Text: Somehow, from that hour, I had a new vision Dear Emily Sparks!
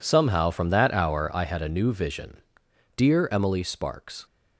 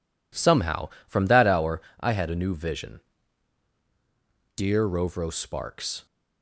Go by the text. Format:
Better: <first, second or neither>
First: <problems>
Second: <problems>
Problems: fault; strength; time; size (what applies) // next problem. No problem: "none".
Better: first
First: pauses between "vision" and "Dear"; noticeable; at 2.3 s; 0.58 s long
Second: pauses between "vision" and "Dear"; strong; at 3.0 s; 1.5 s long // says "Rovro" for "Emily"; at 4.8 s